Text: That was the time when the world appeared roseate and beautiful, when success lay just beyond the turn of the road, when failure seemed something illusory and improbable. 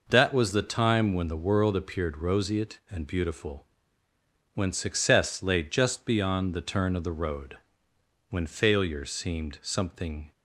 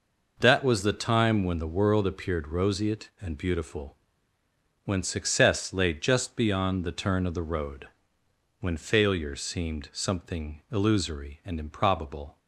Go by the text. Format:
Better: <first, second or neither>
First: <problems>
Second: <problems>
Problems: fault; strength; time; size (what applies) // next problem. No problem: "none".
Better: second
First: stops before "illusory and improbable"; at 10.3 s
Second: none